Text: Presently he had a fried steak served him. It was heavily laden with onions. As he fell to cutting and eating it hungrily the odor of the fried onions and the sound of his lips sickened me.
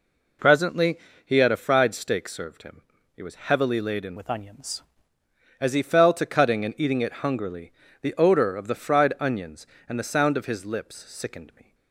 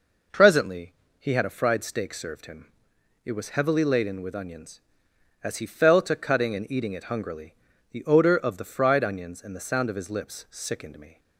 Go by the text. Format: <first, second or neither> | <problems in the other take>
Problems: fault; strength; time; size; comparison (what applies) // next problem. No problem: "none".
second | pauses between "Presently" and "he"; slight; at 0.9 s; 0.26 s long; slight in the second // changes voice from "with" to "onions"; from 4.1 to 4.8 s; 0.7 s long // pauses between "hungrily" and "the"; slight; at 7.7 s; 0.30 s long; slight in the second